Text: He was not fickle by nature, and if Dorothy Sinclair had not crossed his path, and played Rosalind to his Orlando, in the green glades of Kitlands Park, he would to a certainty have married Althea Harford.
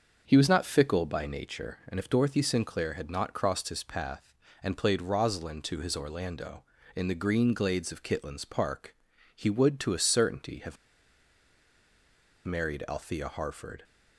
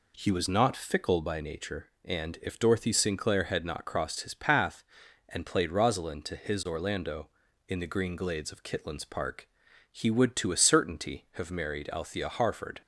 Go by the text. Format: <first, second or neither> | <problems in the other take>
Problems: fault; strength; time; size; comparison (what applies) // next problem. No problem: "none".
second | starts louder than the rest; until 1.2 s; 6.5 dB // pauses between "have" and "married"; strong; at 10.7 s; 1.6 s long